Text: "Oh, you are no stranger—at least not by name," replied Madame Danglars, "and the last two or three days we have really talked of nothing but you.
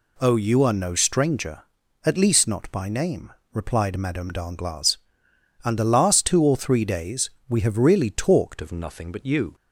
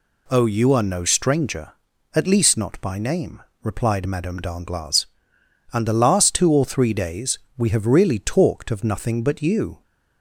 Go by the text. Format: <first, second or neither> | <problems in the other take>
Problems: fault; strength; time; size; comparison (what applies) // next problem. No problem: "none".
second | pauses between "days" and "we"; slight; at 7.2 s; 0.20 s long; slight in the second // changes voice at "of"; from 8.6 s on; 0.9 s long